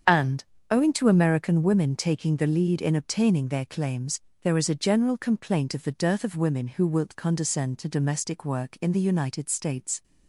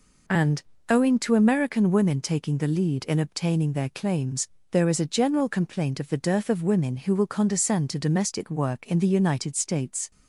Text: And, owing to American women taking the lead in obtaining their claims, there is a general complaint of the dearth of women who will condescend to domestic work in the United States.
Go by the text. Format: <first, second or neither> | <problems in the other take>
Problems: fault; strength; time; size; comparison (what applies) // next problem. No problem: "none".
second | starts louder than the rest; strong; until 1.3 s; 7.5 dB // says "wilt" for "will"; at 6.8 s